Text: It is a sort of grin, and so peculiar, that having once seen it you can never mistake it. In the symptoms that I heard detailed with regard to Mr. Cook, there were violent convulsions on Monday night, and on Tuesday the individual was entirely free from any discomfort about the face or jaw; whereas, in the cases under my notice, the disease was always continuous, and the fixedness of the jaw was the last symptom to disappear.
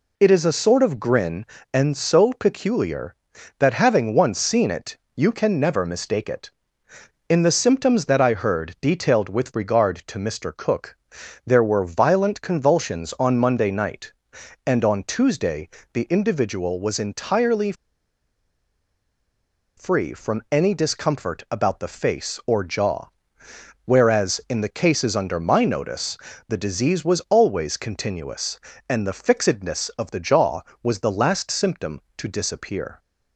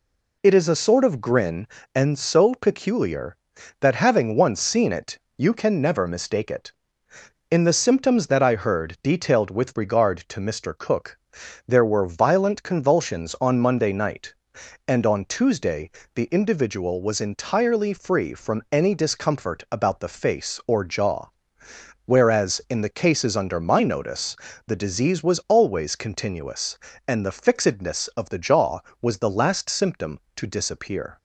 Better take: second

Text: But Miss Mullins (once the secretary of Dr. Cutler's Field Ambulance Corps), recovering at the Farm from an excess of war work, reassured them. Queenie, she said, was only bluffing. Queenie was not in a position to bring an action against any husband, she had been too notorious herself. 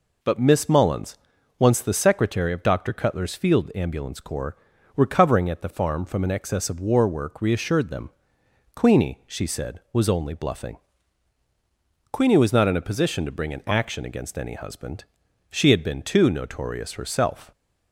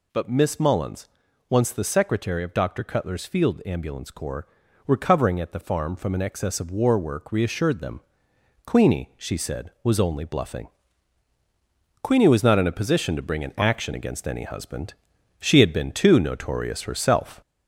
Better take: first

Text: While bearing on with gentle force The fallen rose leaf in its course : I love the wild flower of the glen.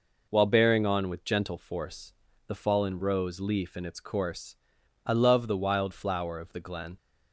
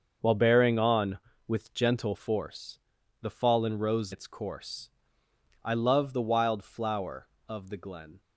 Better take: first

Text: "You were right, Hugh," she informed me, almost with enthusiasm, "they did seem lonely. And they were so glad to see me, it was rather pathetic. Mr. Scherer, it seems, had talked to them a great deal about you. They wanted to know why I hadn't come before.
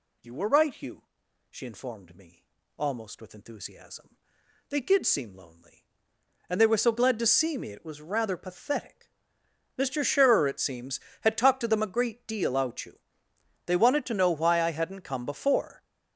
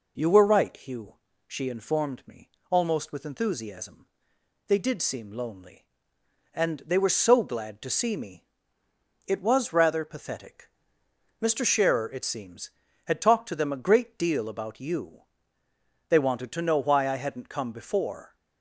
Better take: second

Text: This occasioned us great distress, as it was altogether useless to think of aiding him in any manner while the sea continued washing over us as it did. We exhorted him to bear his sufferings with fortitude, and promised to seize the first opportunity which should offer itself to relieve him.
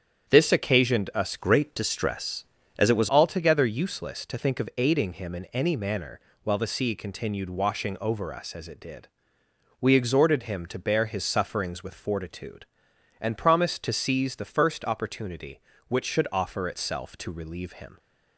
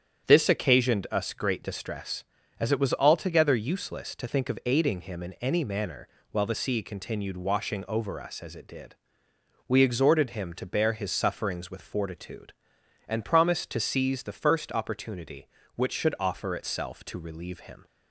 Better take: second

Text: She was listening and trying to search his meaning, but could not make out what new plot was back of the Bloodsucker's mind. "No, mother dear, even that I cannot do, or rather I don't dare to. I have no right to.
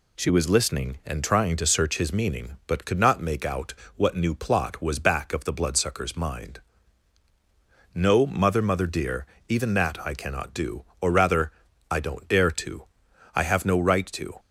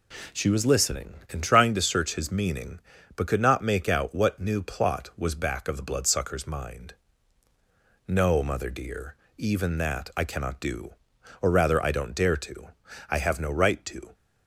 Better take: second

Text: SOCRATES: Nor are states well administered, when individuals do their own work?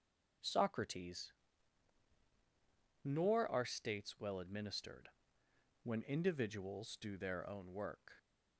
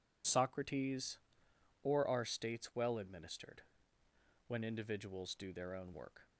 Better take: first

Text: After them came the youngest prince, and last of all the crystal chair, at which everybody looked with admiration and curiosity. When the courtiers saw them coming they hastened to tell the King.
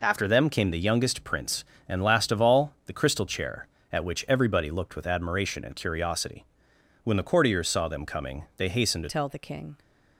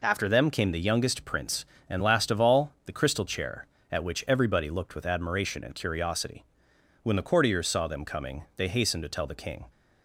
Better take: second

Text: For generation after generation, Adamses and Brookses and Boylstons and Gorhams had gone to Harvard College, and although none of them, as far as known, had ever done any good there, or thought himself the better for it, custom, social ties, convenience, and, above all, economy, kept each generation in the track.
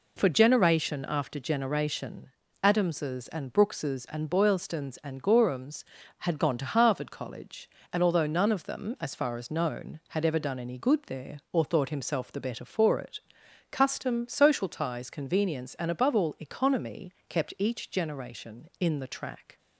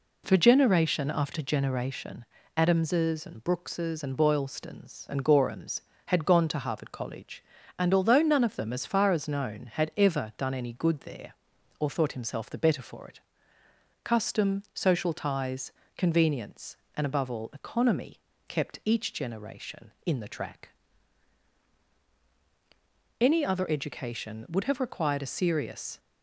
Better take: first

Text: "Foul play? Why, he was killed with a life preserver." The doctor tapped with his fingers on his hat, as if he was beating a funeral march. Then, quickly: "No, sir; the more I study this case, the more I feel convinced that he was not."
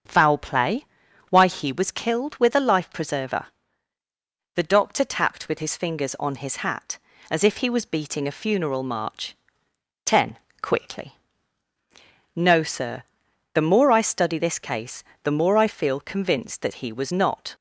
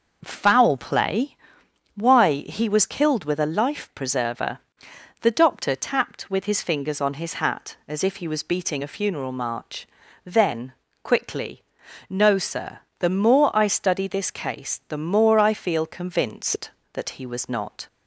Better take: second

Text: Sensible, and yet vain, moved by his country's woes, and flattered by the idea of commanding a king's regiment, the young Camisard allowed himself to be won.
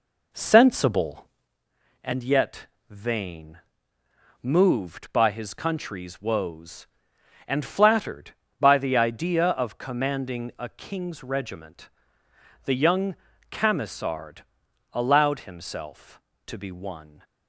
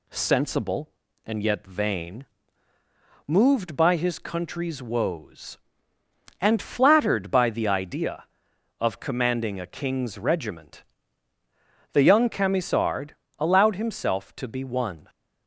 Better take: second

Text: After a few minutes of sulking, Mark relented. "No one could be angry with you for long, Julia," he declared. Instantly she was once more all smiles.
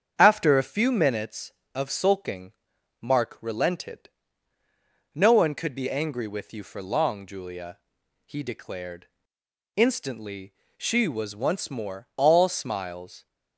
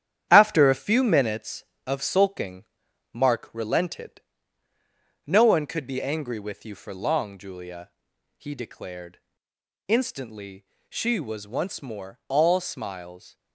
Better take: first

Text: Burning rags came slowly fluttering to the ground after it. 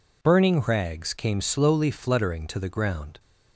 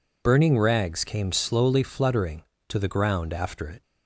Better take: second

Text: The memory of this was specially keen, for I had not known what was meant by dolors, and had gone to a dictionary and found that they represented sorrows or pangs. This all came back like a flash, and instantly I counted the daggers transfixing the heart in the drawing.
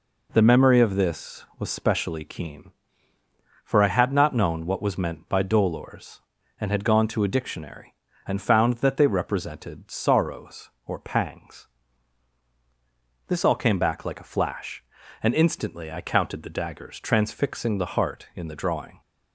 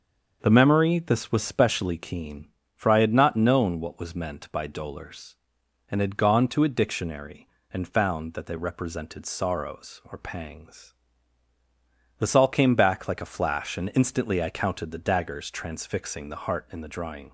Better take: first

